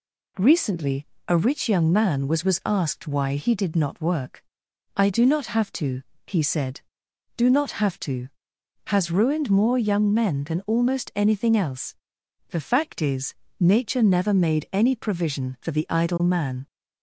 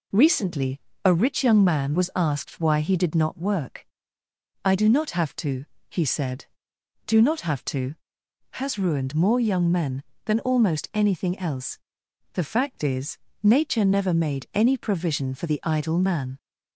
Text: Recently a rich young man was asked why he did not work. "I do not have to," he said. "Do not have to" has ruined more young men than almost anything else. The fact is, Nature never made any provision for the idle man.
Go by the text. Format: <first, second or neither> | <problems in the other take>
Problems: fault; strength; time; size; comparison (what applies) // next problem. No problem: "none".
second | pauses between "Recently" and "a"; slight; at 1.0 s; 0.22 s long; slight in the second // says "was" twice; at 2.4 s